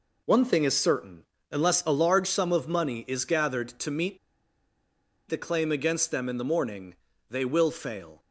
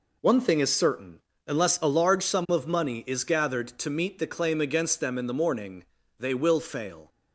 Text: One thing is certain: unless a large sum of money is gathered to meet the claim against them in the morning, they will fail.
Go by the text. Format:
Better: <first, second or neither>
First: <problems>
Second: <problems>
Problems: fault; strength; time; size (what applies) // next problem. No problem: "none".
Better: second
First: pauses between "meet" and "the"; at 4.1 s; 1.1 s long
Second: none